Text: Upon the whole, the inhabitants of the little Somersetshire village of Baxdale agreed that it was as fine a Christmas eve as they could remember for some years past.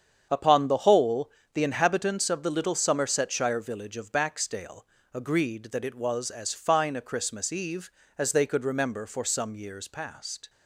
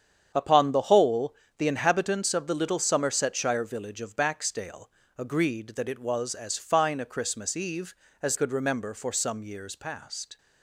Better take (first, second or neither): first